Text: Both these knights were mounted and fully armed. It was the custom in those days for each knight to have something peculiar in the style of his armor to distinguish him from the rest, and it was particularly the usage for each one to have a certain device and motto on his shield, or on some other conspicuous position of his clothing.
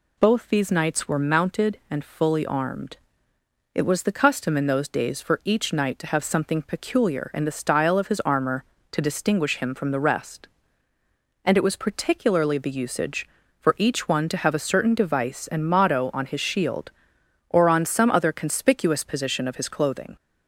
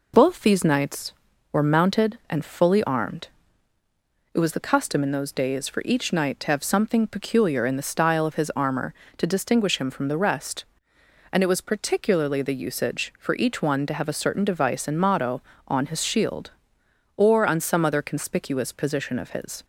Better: first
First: none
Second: stops before "clothing"; at 19.6 s

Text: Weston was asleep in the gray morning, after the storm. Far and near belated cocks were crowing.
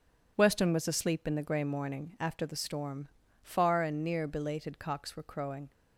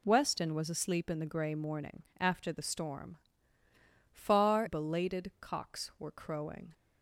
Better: first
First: none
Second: skips "and near"; at 4.6 s

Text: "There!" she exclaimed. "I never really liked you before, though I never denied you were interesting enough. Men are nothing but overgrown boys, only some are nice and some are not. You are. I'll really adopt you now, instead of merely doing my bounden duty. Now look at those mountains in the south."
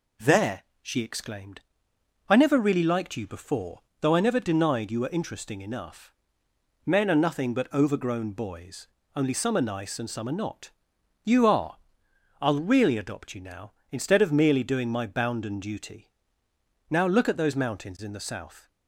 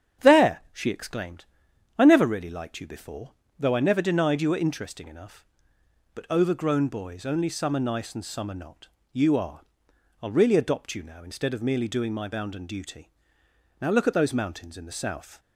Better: first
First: none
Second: starts louder than the rest; strong; until 1.3 s; 8 dB // skips "Men are nothing"; at 5.8 s

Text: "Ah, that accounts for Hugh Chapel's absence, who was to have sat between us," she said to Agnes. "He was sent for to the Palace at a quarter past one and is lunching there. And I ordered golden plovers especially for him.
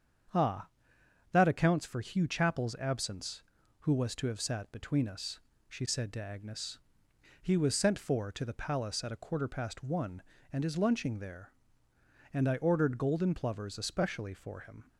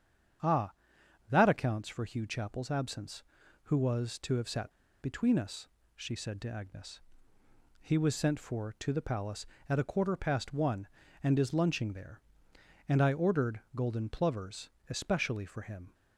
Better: first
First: starts louder than the rest; strong; until 1.9 s; 7.5 dB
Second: starts louder than the rest; strong; until 2.0 s; 8 dB // pauses between "sat" and "between"; slight; at 4.6 s; 0.31 s long // pauses between "plovers" and "especially"; slight; at 14.6 s; 0.22 s long

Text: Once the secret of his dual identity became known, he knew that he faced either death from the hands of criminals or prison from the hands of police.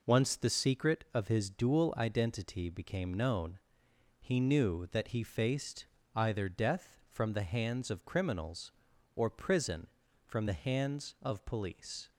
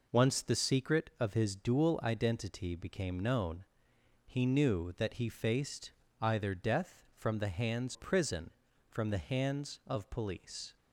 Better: first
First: pauses between "faced" and "either"; slight; at 5.8 s; 0.30 s long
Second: pauses between "faced" and "either"; slight; at 5.9 s; 0.30 s long // skips "of criminals or"; at 7.9 s

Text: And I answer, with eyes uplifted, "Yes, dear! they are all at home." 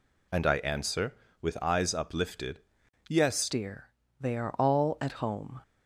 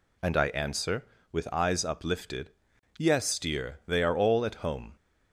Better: second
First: changes voice at "dear"; from 3.4 s on; 2.2 s long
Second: none

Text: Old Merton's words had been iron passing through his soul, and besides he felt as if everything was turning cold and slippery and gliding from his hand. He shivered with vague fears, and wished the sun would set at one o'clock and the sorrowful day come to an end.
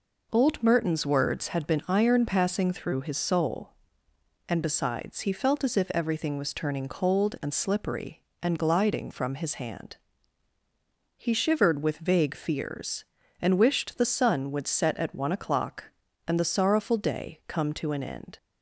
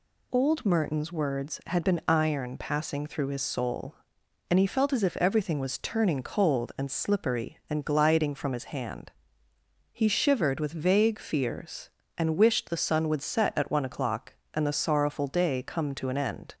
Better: first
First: none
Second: skips "besides"; at 4.5 s

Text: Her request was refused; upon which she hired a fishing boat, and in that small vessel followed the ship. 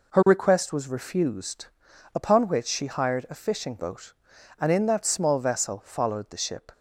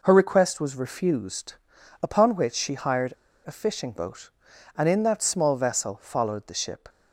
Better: first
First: none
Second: pauses between "hired" and "a"; slight; at 3.1 s; 0.33 s long

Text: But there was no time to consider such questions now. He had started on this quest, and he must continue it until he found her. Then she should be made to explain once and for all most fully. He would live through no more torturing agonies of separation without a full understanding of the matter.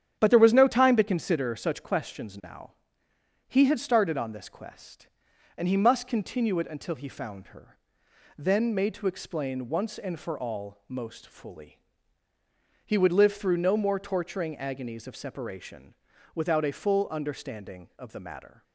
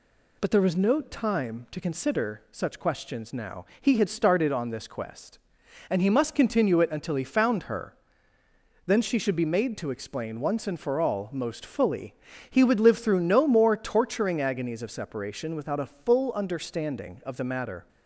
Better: second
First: starts louder than the rest; strong; until 1.2 s; 10 dB // skips "she should be"; at 8.7 s // pauses between "separation" and "without"; at 15.9 s; 0.40 s long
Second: none

